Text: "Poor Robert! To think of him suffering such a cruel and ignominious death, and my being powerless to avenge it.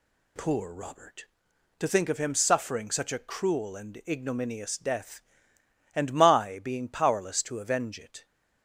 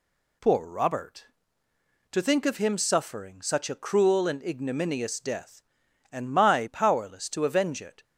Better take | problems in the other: first | skips "being"; at 6.6 s

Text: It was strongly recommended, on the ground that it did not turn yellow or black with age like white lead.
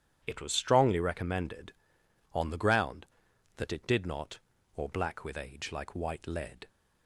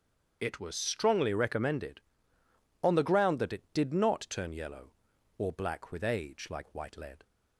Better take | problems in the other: second | starts louder than the rest; strong; until 1.2 s; 10 dB; strong in the second // skips "turn yellow"; at 4.5 s

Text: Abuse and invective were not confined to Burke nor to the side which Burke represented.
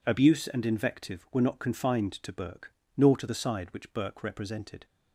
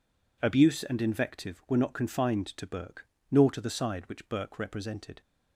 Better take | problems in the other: neither | pauses between "Burke" and "nor"; slight; the same in both

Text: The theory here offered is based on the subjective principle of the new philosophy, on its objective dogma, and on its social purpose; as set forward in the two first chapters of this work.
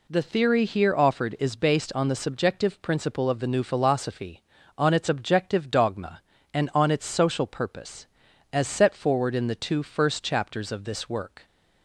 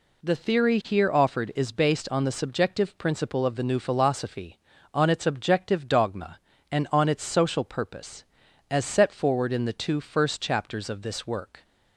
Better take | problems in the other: neither | none

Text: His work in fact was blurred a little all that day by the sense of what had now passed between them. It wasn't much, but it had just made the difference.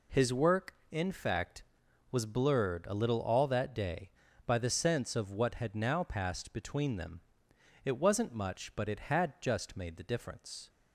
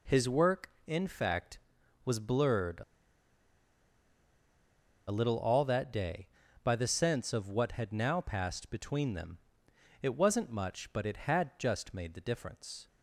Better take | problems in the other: first | pauses between "a" and "little"; strong; at 2.8 s; 2.2 s long

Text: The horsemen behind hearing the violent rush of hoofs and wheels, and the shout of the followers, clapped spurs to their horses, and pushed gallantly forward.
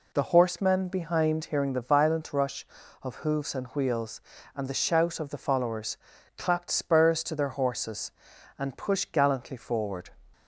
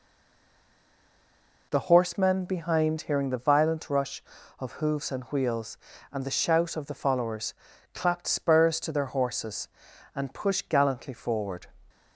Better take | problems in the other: first | stays silent before the first word; noticeable; until 1.7 s; 1.7 s long

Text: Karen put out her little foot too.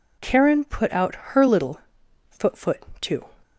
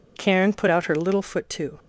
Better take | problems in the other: second | pauses between "little" and "foot"; noticeable; at 1.7 s; 0.52 s long // says "foot" twice; at 2.5 s

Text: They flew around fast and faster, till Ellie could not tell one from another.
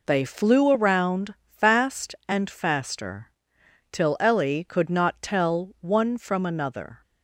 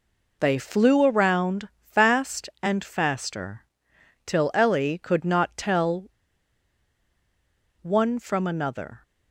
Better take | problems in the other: first | pauses between "tell" and "one"; strong; at 6.0 s; 1.7 s long

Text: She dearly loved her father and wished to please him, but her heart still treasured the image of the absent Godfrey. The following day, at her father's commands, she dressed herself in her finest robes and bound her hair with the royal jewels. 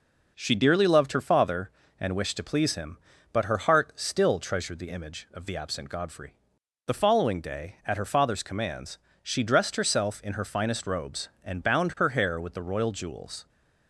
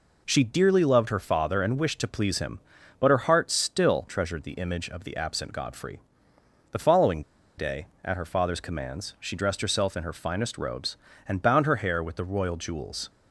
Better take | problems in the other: first | pauses between "following" and "day"; at 7.2 s; 0.36 s long

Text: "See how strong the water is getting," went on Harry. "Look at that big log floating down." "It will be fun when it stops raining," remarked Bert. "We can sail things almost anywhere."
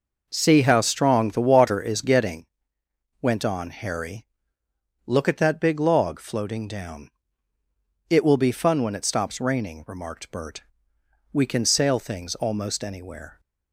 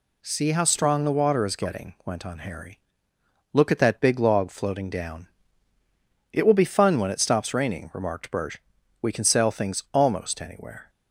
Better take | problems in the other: neither | none

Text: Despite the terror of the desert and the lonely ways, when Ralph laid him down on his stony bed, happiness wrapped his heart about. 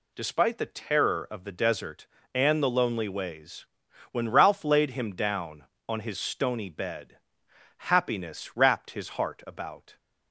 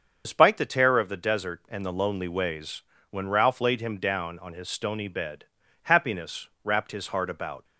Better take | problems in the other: first | loses the start of "Despite"; at 0.2 s; 45 ms // starts louder than the rest; until 1.2 s; 6.5 dB // pauses between "happiness" and "wrapped"; slight; at 6.4 s; 0.16 s long

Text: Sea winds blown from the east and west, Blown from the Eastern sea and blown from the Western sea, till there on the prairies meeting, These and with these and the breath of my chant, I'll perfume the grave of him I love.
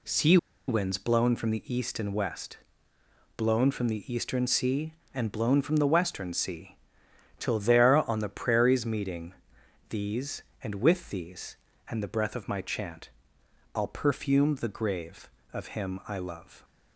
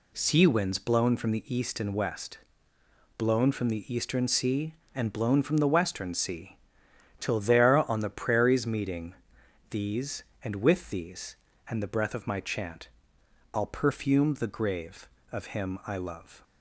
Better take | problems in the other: second | pauses between "Sea" and "winds"; slight; at 0.3 s; 0.31 s long

